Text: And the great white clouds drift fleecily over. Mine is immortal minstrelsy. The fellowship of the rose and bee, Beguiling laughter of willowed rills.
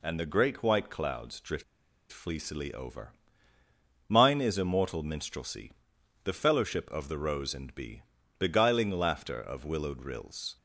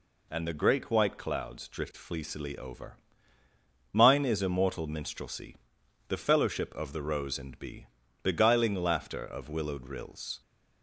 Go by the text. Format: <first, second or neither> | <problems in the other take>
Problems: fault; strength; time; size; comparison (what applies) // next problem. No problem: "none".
second | pauses between "drift" and "fleecily"; noticeable; at 1.6 s; 0.48 s long